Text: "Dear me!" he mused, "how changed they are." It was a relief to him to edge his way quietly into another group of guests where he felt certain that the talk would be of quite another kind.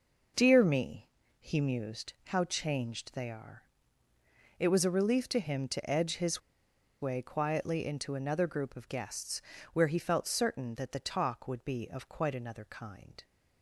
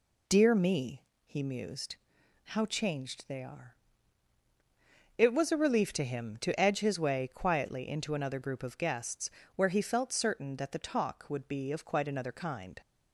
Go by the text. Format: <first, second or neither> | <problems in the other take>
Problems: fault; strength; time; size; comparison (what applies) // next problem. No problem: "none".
second | pauses between "his" and "way"; noticeable; at 6.4 s; 0.61 s long // pauses between "guests" and "where"; slight; at 9.4 s; 0.32 s long; slight in the second